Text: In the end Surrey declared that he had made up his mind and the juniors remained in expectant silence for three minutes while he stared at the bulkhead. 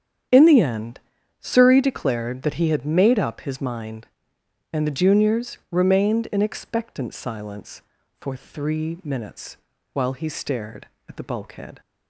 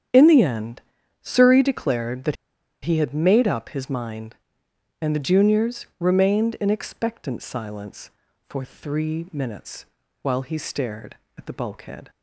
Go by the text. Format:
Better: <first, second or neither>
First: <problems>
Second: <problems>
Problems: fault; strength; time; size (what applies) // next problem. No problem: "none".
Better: first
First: starts louder than the rest; strong; until 1.7 s; 9 dB // pauses between "end" and "Surrey"; at 0.9 s; 0.40 s long // pauses between "minutes" and "while"; slight; at 9.5 s; 0.35 s long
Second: starts louder than the rest; strong; until 1.5 s; 9 dB // pauses between "end" and "Surrey"; at 0.8 s; 0.40 s long // pauses between "that" and "he"; noticeable; at 2.3 s; 0.48 s long // pauses between "minutes" and "while"; slight; at 9.8 s; 0.36 s long